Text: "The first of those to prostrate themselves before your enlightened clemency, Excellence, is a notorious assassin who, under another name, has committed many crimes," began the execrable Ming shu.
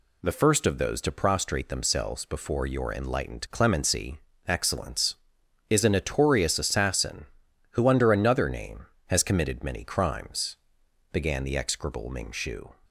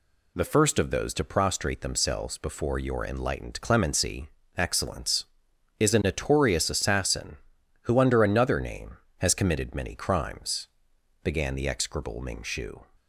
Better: neither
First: none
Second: none

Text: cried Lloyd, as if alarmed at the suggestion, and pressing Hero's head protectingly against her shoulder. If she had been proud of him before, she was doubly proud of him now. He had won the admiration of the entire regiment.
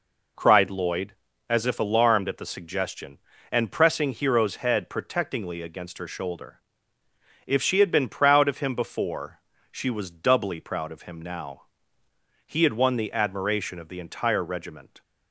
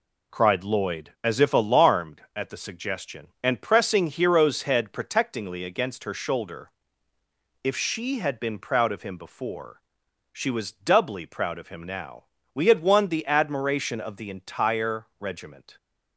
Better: first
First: none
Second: says "We" for "He"; at 12.5 s

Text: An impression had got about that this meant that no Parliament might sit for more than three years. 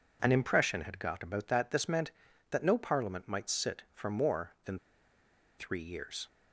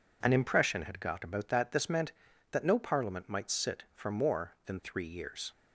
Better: second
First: pauses between "than" and "three"; noticeable; at 4.7 s; 0.81 s long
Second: none

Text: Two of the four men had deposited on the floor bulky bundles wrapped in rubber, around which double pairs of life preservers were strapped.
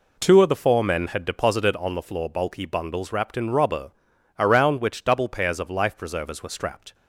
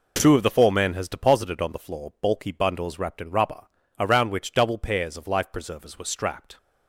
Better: first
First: none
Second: says "has" for "had"; at 0.9 s

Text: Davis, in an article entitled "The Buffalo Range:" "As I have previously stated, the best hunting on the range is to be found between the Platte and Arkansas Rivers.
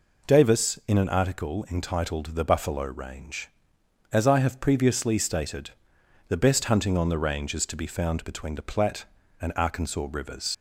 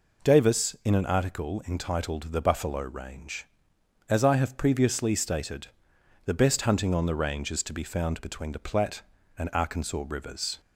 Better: second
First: leaves "Rivers" unfinished; at 10.5 s; 80 ms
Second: none

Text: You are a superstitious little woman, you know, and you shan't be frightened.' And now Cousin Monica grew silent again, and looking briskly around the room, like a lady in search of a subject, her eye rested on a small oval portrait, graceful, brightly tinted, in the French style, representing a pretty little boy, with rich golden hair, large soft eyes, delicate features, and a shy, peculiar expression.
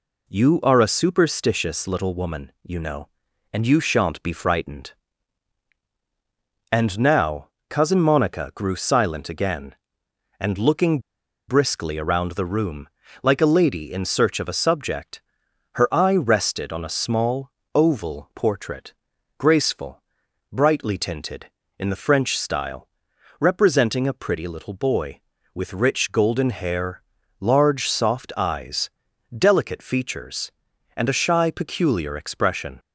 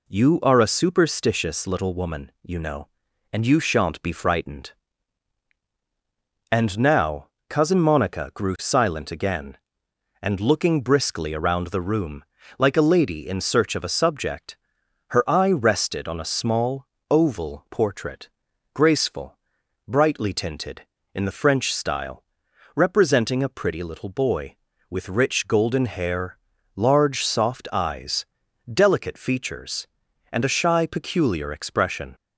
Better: second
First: pauses between "now" and "Cousin"; slight; at 7.4 s; 0.20 s long // pauses between "looking" and "briskly"; noticeable; at 10.9 s; 0.49 s long // pauses between "small" and "oval"; slight; at 17.5 s; 0.24 s long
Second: pauses between "now" and "Cousin"; slight; at 7.2 s; 0.20 s long // pauses between "small" and "oval"; slight; at 16.8 s; 0.24 s long

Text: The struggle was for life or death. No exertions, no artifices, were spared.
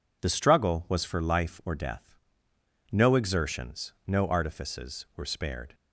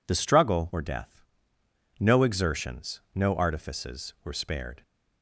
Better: first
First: none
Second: skips "was for life"; at 0.6 s

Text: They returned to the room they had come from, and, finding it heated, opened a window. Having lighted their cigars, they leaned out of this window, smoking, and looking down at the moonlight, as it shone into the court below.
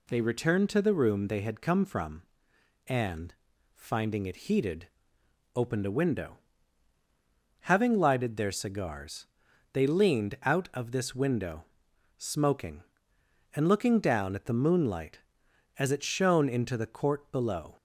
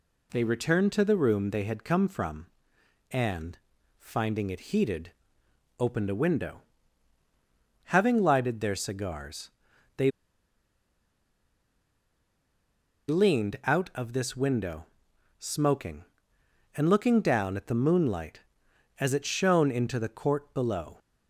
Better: first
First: none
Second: pauses between "they" and "leaned"; strong; at 10.1 s; 2.9 s long

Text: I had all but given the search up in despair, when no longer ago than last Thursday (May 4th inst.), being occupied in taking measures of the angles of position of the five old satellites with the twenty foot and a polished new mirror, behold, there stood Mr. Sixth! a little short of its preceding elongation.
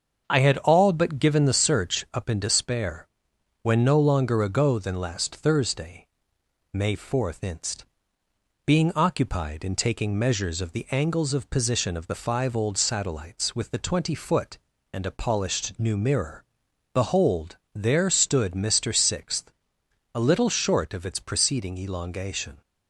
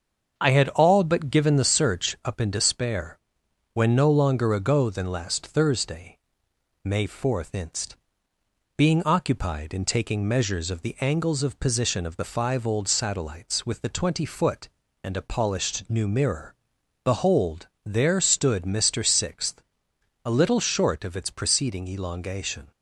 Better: neither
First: starts louder than the rest; until 1.2 s; 7 dB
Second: starts louder than the rest; until 1.4 s; 7 dB

